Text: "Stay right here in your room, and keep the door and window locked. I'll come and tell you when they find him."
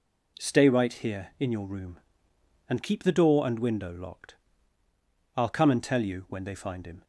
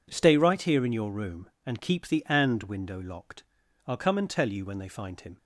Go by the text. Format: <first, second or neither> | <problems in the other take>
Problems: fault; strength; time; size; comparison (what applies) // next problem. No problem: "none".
first | skips "door"; at 2.2 s